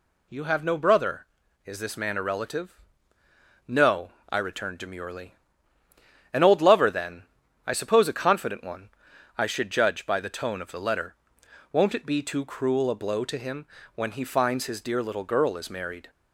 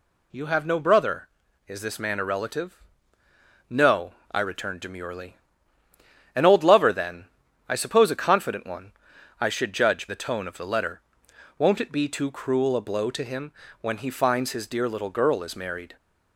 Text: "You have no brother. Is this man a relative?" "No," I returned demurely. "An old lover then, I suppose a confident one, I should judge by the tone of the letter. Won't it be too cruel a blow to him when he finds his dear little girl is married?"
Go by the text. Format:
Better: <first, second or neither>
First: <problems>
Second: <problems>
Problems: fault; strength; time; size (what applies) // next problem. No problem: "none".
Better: first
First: pauses between "him" and "when"; slight; at 13.6 s; 0.30 s long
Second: skips "by"; at 10.0 s // pauses between "him" and "when"; slight; at 13.5 s; 0.30 s long